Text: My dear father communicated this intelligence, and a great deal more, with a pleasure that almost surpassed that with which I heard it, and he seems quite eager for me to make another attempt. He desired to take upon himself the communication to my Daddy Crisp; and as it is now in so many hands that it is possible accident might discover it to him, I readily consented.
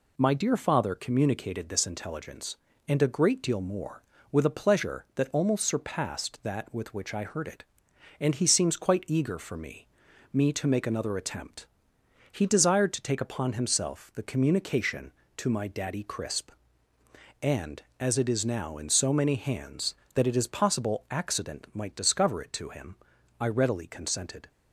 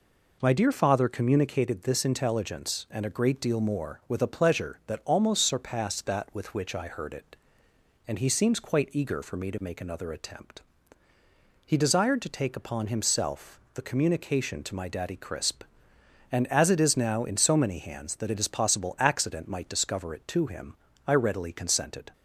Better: second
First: says "me" twice; at 10.3 s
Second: none

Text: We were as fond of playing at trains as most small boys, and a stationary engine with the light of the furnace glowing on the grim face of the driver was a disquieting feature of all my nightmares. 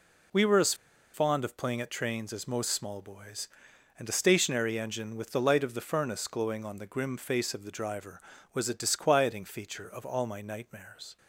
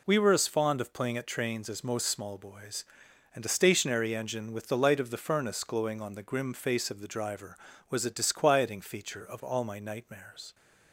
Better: second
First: pauses between "as" and "fond"; at 0.7 s; 0.39 s long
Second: none

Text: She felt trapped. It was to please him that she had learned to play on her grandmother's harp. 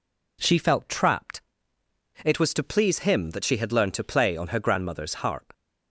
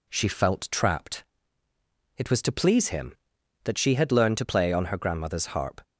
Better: neither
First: none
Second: none

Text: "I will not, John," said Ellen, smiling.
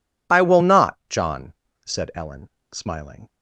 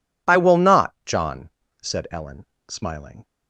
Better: neither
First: none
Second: none

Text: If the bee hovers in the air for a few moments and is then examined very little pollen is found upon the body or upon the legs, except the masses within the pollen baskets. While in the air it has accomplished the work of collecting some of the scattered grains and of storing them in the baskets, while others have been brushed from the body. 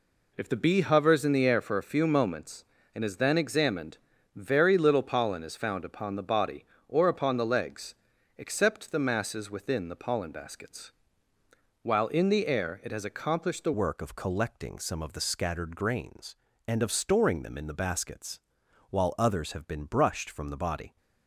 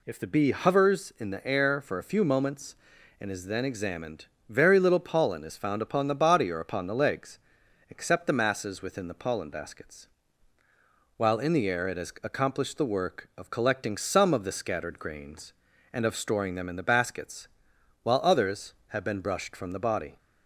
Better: second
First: pauses between "examined" and "very"; slight; at 3.9 s; 0.36 s long // changes voice at "work"; from 13.7 s on; 7.2 s long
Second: pauses between "examined" and "very"; slight; at 4.2 s; 0.22 s long

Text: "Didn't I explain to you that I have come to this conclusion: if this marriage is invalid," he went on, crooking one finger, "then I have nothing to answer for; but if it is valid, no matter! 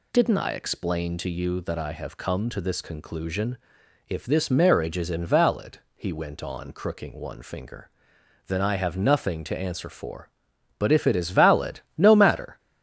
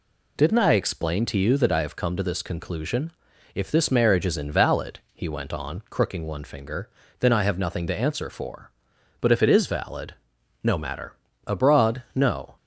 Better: first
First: none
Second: goes on to say "Abroad no"; noticeable; from 11.4 s on; 1.1 s long

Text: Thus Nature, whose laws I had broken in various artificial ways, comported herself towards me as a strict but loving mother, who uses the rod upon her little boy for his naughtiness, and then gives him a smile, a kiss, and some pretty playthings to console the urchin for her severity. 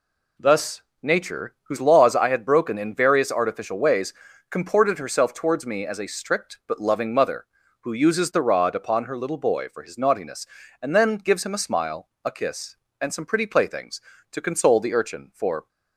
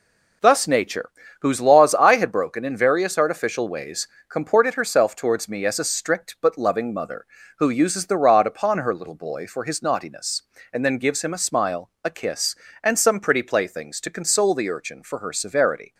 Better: second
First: pauses between "Thus" and "Nature"; slight; at 0.8 s; 0.20 s long // stops before "her severity"; at 15.6 s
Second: none

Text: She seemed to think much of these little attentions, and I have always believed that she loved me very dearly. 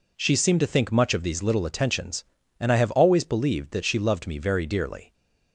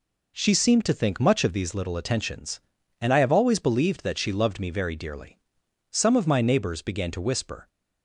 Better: first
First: none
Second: goes on to say "Some of my neighbors began to whisper"; strong; from 5.9 s on; 1.7 s long

